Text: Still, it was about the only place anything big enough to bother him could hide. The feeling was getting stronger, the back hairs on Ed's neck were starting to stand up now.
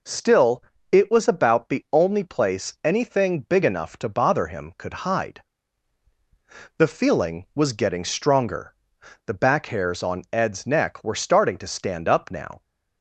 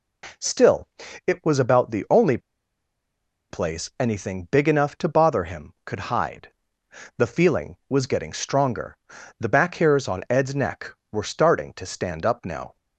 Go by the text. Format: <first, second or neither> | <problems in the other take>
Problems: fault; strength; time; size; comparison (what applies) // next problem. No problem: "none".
first | pauses between "only" and "place"; at 2.3 s; 1.1 s long